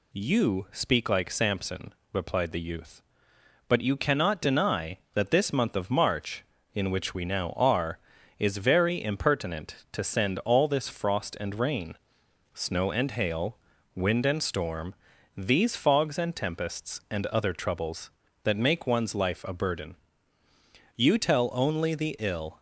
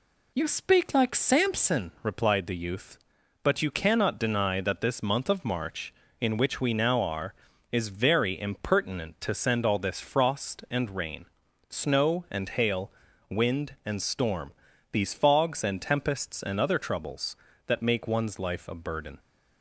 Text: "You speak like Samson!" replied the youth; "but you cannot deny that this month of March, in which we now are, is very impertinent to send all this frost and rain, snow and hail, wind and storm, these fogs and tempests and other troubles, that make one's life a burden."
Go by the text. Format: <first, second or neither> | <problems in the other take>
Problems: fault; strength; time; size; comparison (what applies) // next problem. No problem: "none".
second | goes on to say "You tell only the ill"; from 20.9 s on; 1.6 s long